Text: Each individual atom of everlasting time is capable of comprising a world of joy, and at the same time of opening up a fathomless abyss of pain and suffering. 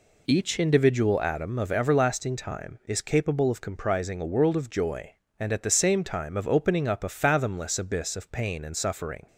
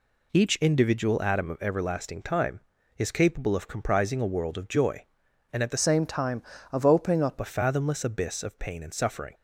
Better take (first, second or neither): first